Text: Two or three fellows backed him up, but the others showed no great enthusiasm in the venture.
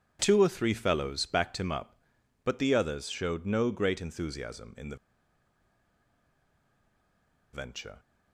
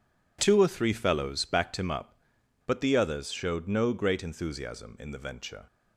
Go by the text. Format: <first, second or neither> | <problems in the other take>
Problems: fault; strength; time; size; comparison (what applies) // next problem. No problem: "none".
second | pauses between "the" and "venture"; strong; at 4.9 s; 2.5 s long